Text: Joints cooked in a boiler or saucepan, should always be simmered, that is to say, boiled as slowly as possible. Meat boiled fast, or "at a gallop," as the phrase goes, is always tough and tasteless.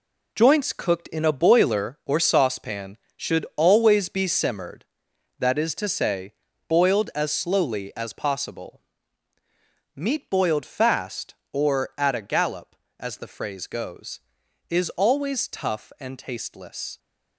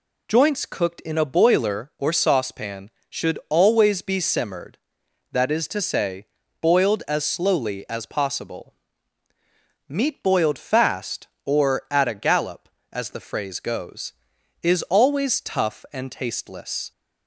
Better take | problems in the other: second | gets quieter; strong; throughout; 8 dB

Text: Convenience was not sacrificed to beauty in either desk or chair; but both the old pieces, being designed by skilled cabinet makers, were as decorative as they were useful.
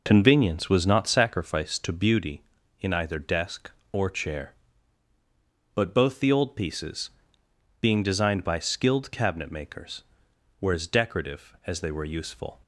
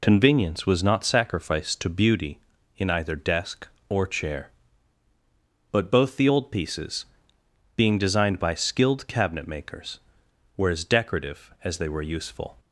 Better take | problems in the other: second | starts louder than the rest; noticeable; until 1.5 s; 4.5 dB

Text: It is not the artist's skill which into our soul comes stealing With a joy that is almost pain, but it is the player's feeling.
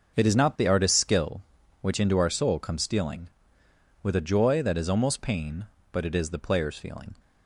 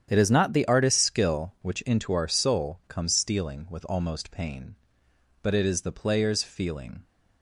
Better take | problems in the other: first | starts louder than the rest; strong; until 1.1 s; 9 dB; also in the first // skips "a joy that is"; at 3.8 s

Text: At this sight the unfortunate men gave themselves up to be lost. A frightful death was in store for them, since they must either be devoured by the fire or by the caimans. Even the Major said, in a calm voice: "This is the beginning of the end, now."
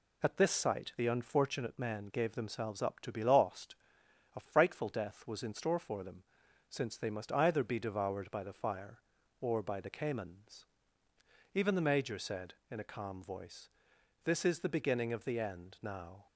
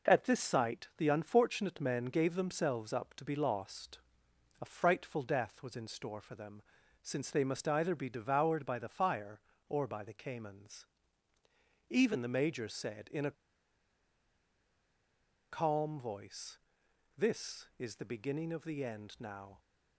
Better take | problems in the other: first | pauses between "a" and "calm"; strong; at 13.3 s; 2.1 s long

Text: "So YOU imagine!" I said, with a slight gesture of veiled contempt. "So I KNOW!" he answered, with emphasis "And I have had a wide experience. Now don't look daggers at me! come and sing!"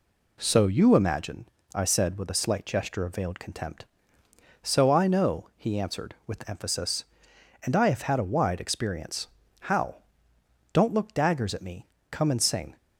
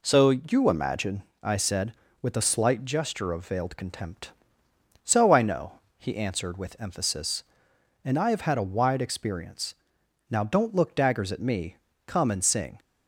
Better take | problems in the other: second | says "How" for "Now"; at 9.6 s

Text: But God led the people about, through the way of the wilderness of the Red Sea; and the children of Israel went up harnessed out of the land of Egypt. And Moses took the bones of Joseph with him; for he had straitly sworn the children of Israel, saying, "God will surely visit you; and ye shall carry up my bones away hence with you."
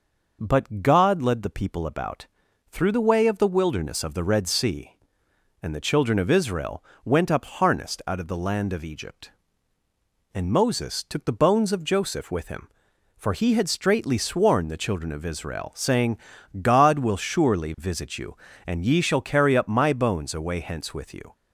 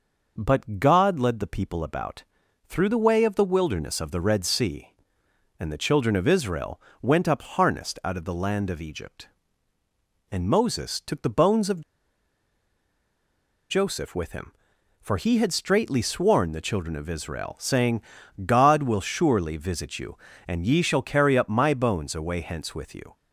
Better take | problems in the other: first | pauses between "Israel" and "went"; slight; at 6.7 s; 0.22 s long; slight in the first // pauses between "of" and "Joseph"; strong; at 11.8 s; 1.8 s long

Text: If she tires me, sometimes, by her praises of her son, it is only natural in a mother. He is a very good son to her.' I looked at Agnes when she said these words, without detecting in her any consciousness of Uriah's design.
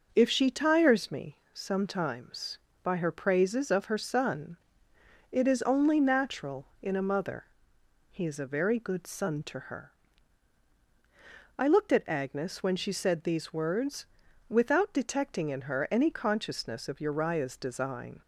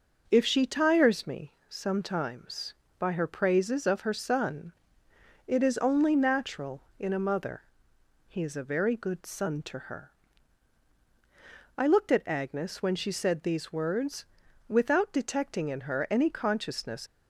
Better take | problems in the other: first | stops before "of Uriah's design"; at 17.0 s

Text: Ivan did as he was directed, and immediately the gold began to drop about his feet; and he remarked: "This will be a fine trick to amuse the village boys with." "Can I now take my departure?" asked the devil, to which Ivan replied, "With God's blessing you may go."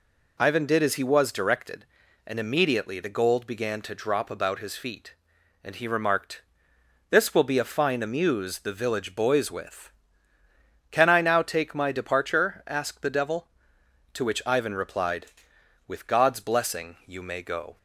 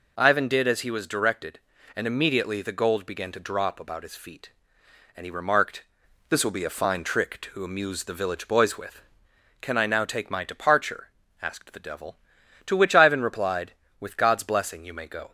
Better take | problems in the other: second | skips "trick to"; at 8.0 s

